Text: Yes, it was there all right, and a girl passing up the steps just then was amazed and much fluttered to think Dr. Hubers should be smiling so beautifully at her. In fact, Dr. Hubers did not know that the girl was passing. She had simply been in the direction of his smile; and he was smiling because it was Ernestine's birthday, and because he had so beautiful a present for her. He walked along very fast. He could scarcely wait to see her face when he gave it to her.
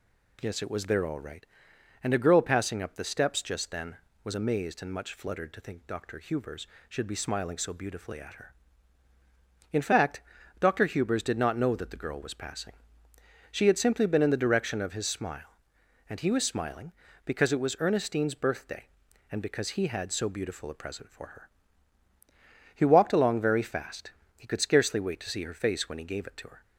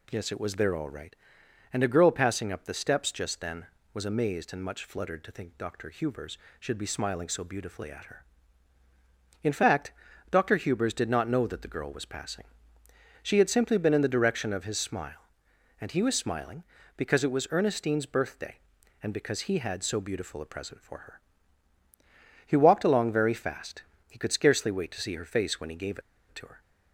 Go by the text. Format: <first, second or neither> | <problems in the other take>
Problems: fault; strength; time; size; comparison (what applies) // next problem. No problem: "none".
first | pauses between "gave" and "it"; slight; at 25.9 s; 0.29 s long